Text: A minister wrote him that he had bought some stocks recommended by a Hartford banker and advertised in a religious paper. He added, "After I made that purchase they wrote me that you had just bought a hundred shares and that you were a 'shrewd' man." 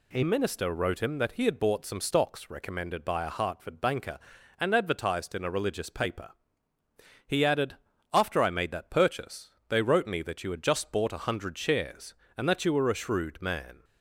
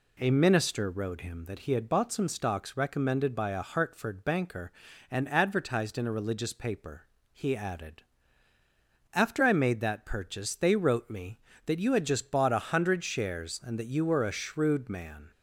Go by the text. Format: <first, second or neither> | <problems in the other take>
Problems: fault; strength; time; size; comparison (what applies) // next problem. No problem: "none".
second | changes voice at "minister"; from 0.2 s on; 13.6 s long // pauses between "purchase" and "they"; slight; at 9.5 s; 0.18 s long